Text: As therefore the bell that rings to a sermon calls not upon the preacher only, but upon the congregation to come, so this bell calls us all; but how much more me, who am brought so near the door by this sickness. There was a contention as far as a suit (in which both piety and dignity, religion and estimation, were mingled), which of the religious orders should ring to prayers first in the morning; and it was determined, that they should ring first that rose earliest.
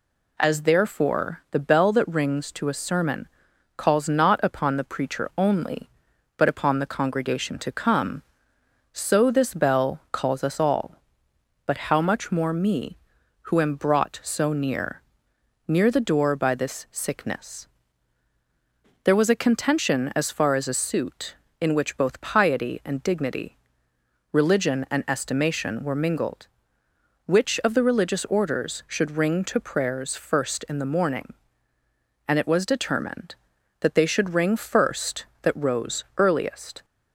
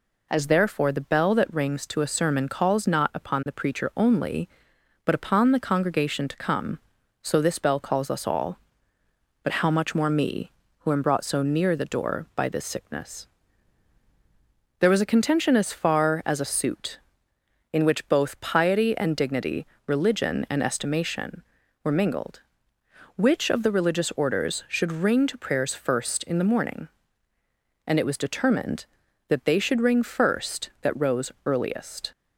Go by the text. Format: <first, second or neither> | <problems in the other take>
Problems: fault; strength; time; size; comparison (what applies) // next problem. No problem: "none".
second | pauses between "sermon" and "calls"; noticeable; at 3.2 s; 0.50 s long // says "near" twice; at 15.6 s